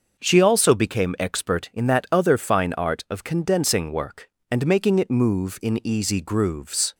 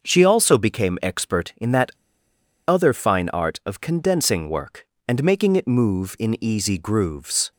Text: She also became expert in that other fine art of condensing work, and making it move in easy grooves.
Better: first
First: starts louder than the rest; until 1.2 s; 6 dB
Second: starts louder than the rest; until 1.0 s; 6 dB // pauses between "that" and "other"; noticeable; at 1.9 s; 0.76 s long

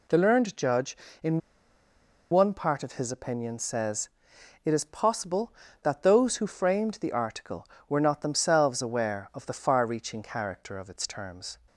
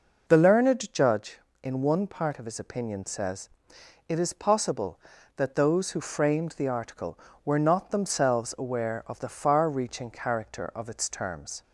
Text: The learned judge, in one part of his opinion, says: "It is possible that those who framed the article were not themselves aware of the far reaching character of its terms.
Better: second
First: pauses between "in" and "one"; noticeable; at 1.3 s; 0.91 s long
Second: none

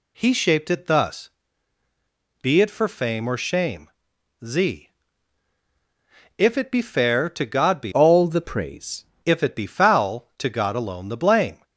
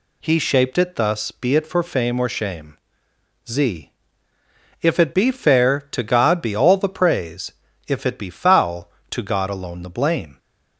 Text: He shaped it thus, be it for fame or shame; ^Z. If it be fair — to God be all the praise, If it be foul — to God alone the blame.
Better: second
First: changes voice from "all" to "praise"; from 7.9 to 9.0 s; 1.1 s long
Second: none

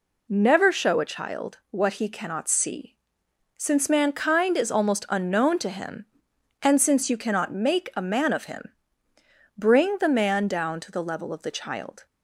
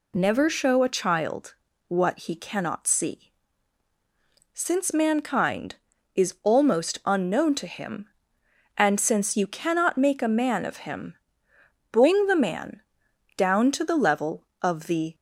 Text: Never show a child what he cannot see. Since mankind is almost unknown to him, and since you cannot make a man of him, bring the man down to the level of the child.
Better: first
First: none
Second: pauses between "child" and "what"; slight; at 1.5 s; 0.34 s long // pauses between "man" and "down"; noticeable; at 12.8 s; 0.54 s long // stops before "child"; at 15.1 s

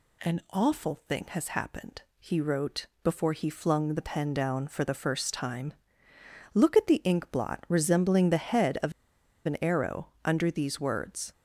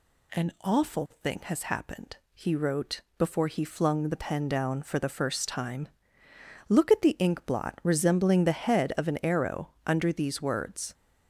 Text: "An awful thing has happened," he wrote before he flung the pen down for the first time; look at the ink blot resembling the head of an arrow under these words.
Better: second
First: pauses between "wrote" and "before"; slight; at 2.8 s; 0.16 s long // pauses between "of" and "an"; noticeable; at 8.9 s; 0.55 s long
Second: pauses between "wrote" and "before"; slight; at 3.0 s; 0.16 s long

